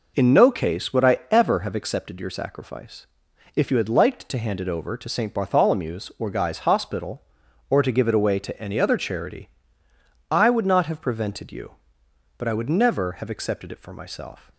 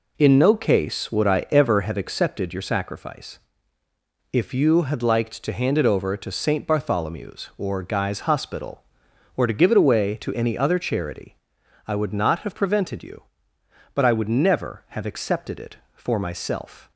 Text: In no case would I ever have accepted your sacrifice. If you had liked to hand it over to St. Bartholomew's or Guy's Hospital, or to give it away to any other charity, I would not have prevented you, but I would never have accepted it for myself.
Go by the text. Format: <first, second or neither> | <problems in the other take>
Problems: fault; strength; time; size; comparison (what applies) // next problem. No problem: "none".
neither | none